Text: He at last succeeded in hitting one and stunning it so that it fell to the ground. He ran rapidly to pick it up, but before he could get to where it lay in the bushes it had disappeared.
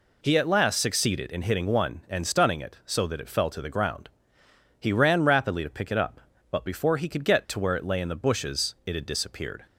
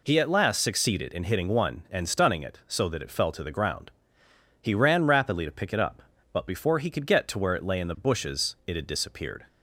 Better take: neither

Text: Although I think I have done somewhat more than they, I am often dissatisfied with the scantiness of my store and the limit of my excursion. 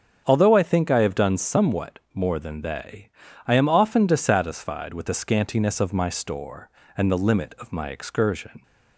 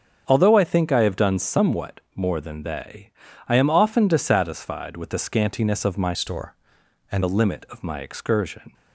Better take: first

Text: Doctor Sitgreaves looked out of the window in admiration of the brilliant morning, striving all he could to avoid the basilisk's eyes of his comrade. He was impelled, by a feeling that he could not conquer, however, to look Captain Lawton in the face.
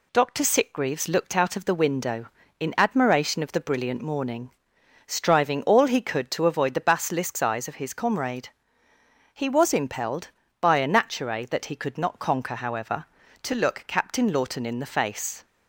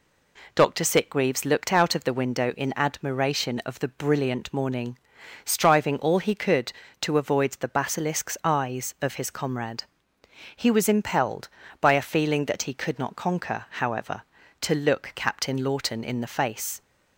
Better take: second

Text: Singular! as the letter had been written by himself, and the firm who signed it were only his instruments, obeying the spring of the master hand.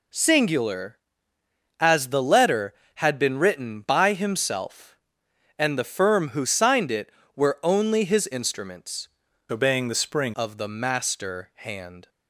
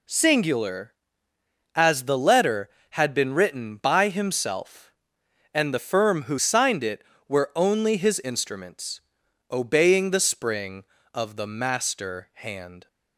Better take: second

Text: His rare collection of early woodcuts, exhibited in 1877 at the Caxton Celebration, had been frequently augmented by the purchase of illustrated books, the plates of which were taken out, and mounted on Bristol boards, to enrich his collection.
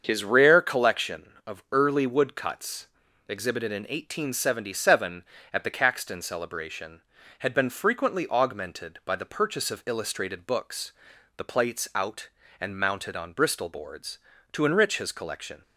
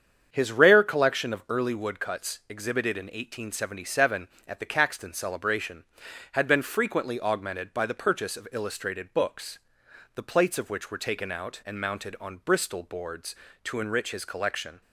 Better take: second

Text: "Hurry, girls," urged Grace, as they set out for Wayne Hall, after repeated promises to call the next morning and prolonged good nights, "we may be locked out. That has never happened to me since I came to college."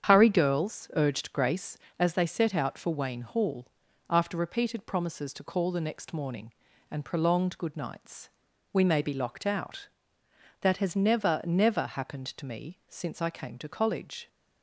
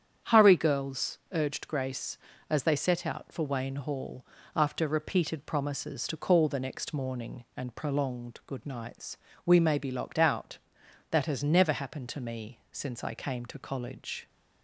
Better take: second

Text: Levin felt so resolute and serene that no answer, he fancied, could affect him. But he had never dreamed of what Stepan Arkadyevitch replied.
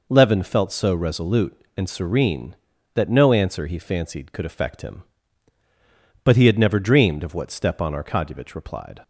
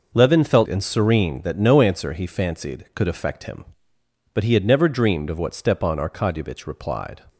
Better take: first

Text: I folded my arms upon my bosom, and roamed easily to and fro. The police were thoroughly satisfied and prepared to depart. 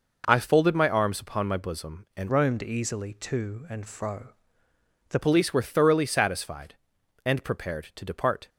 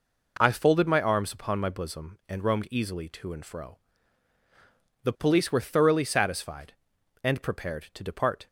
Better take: second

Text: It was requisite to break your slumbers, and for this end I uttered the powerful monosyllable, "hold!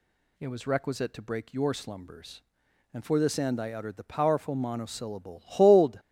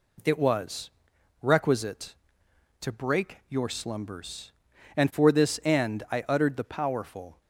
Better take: first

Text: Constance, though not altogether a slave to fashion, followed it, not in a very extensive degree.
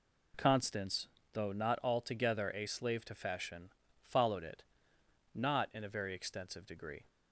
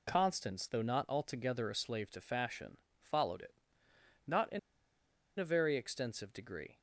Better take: first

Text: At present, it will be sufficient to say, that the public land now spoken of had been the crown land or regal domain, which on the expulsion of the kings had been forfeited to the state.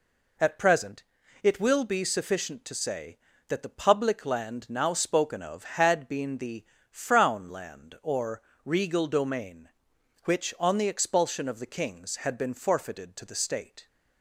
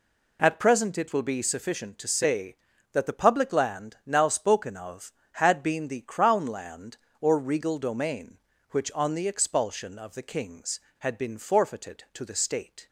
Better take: second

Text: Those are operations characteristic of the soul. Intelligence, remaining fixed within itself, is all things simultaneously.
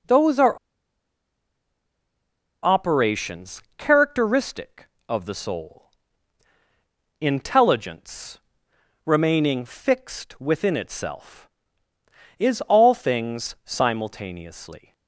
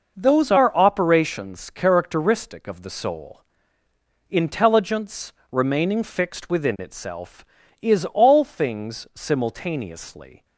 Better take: second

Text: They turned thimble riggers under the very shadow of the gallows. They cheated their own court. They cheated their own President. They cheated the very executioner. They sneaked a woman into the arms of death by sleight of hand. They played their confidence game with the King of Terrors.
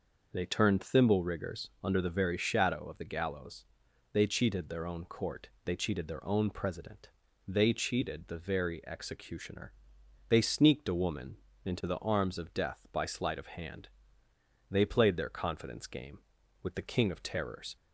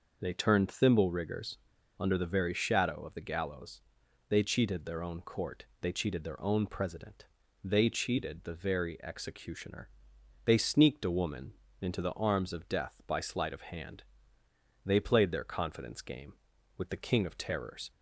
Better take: first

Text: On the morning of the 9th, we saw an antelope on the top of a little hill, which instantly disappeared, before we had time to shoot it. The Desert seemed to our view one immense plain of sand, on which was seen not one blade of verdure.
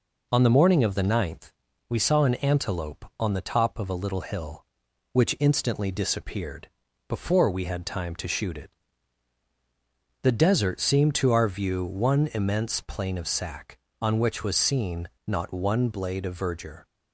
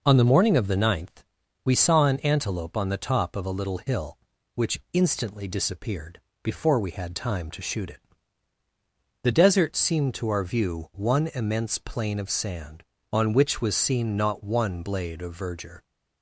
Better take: second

